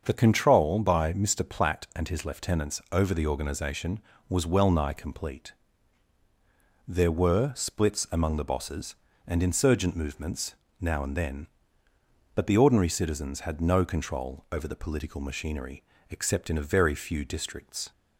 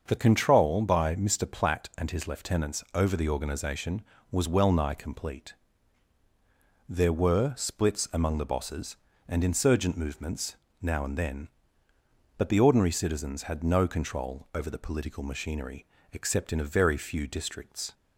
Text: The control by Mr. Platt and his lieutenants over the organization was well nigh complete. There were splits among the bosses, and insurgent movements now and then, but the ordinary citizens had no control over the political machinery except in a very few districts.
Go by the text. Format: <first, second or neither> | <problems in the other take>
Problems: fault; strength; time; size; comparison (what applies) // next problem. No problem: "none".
neither | starts louder than the rest; the same in both // pauses between "movements" and "now"; slight; the same in both // pauses between "machinery" and "except"; slight; the same in both